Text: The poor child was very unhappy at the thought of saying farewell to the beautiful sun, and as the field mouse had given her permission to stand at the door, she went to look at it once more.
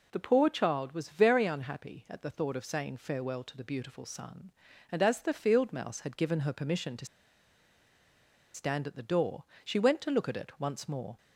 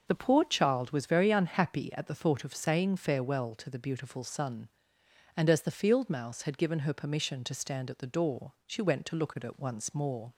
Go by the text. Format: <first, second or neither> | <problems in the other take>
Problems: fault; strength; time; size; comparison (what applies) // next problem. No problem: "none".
second | pauses between "to" and "stand"; strong; at 7.0 s; 1.4 s long